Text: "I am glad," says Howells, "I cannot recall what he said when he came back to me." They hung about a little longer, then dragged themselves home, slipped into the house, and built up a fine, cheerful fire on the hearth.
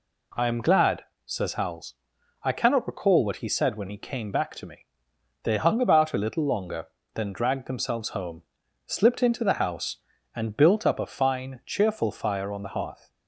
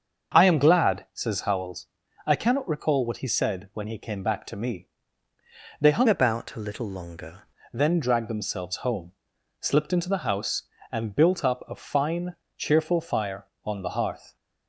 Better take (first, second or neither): first